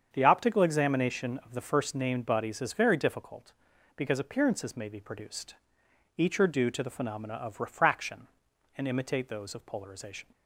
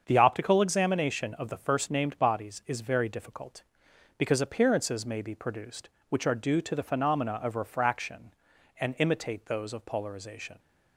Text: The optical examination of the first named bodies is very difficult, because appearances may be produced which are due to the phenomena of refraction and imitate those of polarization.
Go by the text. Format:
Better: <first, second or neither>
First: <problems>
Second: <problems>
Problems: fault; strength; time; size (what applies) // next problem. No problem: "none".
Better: second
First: starts louder than the rest; strong; until 1.1 s; 7.5 dB // says "each" for "which"; at 6.1 s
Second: starts louder than the rest; strong; until 1.0 s; 7 dB